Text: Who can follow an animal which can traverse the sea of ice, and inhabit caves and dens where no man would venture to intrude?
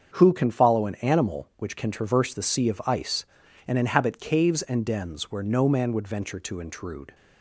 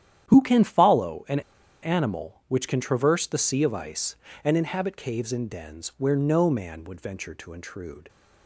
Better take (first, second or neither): first